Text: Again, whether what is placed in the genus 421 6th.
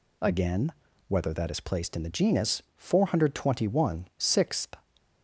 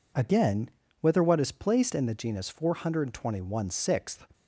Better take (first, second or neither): second